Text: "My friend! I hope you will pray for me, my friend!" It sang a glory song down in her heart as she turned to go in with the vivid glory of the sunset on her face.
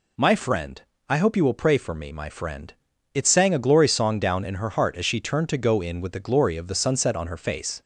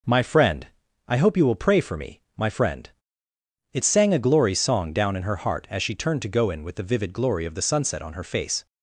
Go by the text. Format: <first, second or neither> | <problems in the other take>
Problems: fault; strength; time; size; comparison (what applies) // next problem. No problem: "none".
second | skips "vivid"; at 6.1 s